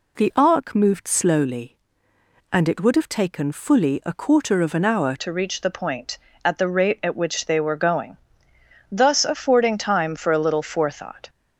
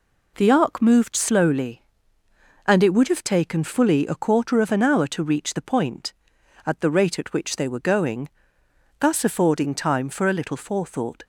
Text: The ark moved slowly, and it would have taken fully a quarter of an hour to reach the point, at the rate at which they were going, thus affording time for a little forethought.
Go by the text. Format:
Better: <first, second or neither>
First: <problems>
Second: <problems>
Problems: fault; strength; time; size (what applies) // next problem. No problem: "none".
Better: second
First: changes voice at "to"; from 5.1 s on; 6.1 s long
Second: none